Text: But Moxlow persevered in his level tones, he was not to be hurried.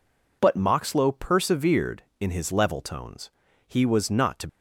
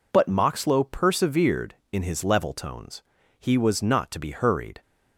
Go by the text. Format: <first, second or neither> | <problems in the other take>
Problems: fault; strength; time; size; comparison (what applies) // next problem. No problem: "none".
second | stops before "be hurried"; at 4.4 s